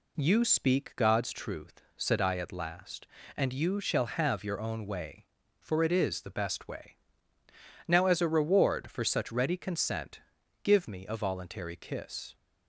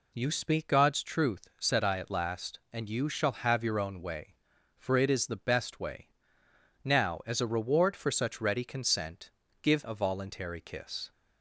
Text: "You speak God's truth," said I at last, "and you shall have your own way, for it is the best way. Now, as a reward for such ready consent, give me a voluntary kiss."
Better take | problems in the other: first | skips "me"; at 9.8 s

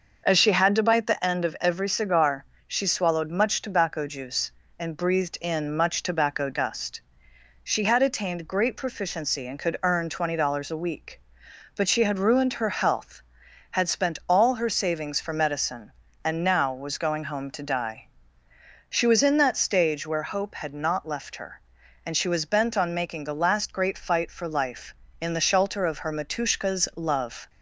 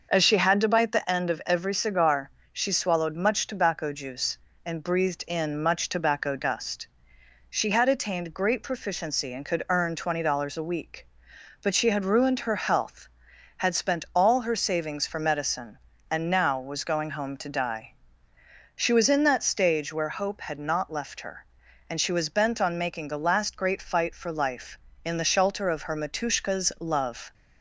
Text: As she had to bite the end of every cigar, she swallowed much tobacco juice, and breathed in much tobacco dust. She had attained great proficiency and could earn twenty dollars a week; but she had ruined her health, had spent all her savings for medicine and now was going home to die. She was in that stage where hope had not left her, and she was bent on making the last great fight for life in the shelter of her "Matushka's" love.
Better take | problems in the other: neither | starts louder than the rest; noticeable; the same in both

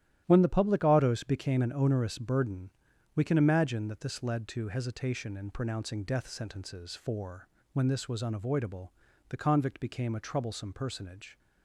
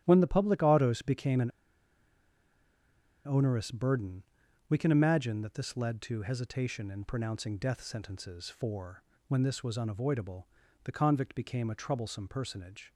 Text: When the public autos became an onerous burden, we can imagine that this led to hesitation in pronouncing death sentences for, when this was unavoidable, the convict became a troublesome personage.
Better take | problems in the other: first | starts louder than the rest; strong; until 1.0 s; 12.5 dB; strong in the first // pauses between "an" and "onerous"; strong; at 1.5 s; 1.7 s long

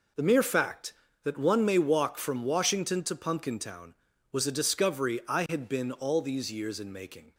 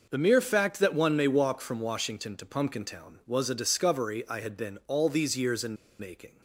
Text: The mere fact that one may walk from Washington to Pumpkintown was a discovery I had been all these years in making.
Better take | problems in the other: first | pauses between "in" and "making"; slight; at 5.7 s; 0.23 s long

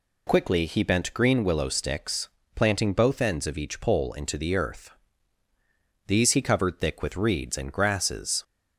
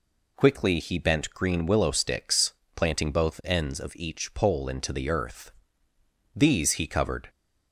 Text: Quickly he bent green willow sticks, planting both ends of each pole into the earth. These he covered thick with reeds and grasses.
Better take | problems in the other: first | stops before "thick with reeds and grasses"; at 7.2 s

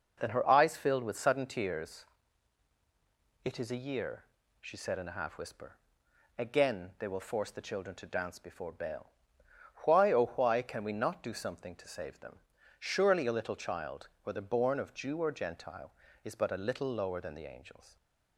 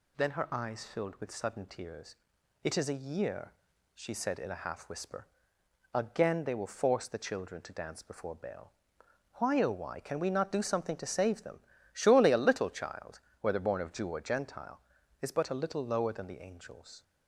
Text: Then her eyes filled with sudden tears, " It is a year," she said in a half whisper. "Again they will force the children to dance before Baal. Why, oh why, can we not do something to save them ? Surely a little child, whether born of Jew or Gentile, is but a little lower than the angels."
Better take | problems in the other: neither | none

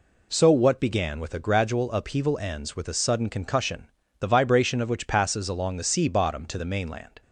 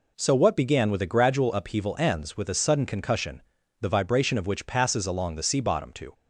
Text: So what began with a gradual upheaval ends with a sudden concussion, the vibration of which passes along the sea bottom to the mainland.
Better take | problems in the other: first | stops before "the mainland"; at 6.1 s

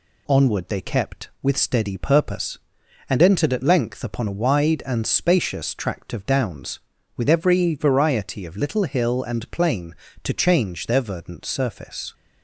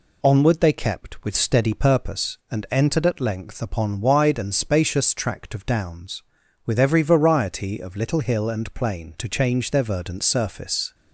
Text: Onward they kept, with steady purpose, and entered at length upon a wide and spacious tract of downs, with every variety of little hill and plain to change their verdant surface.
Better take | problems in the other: first | skips "a"; at 4.0 s

